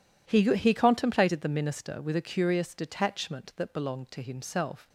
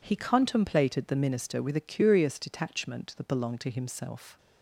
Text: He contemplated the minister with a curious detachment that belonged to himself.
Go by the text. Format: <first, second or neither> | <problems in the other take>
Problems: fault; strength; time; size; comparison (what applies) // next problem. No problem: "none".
second | says "He" twice; at 0.5 s